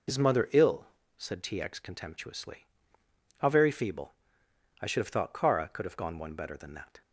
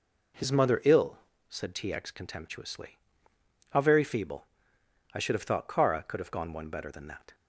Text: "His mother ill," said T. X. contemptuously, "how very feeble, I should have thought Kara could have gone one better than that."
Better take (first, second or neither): second